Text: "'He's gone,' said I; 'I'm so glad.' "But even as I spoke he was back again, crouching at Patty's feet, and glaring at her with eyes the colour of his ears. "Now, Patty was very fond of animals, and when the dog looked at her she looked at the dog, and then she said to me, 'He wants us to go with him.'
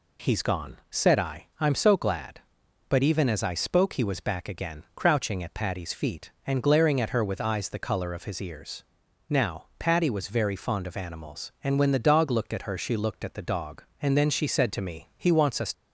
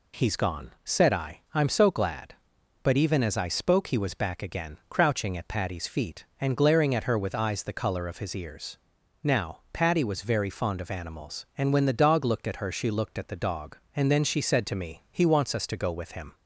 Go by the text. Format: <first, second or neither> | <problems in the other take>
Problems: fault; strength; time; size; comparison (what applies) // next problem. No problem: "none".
second | stops before "to go with him"; at 15.7 s